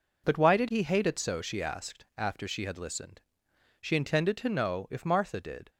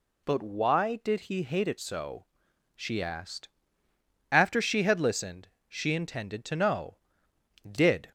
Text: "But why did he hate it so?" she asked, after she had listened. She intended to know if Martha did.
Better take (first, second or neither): first